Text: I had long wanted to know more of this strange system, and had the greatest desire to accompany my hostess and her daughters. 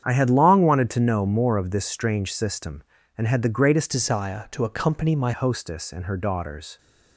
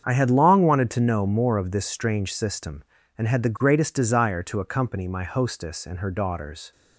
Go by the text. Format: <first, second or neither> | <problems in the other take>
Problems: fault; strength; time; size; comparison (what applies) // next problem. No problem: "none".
second | starts louder than the rest; strong; until 1.0 s; 8.5 dB; strong in the second // changes voice from "desire" to "my"; from 3.8 to 5.3 s; 1.5 s long